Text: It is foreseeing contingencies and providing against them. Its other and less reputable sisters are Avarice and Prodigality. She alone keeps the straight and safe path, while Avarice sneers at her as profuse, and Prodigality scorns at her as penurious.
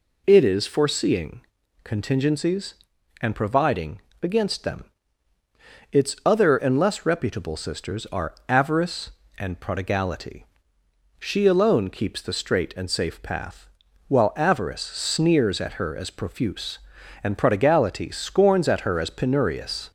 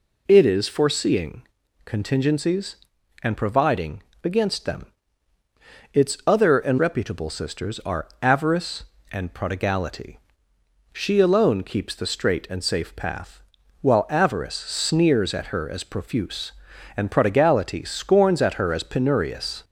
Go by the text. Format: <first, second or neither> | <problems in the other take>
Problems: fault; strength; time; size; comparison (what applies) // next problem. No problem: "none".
first | pauses between "foreseeing" and "contingencies"; at 1.4 s; 0.42 s long; also in the first // pauses between "providing" and "against"; slight; at 4.0 s; 0.22 s long; slight in the first // skips "less"; at 6.7 s // pauses between "are" and "Avarice"; slight; at 8.0 s; 0.16 s long; slight in the first